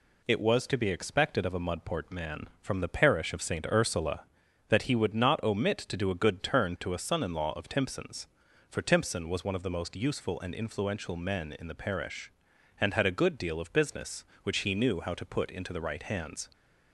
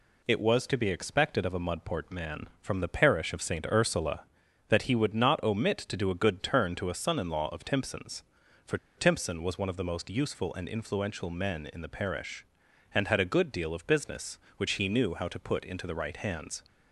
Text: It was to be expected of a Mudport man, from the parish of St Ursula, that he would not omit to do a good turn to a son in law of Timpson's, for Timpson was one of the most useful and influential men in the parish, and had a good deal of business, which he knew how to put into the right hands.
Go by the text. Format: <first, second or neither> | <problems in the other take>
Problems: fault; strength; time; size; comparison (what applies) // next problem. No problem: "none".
first | pauses between "for" and "Timpson"; slight; at 8.7 s; 0.20 s long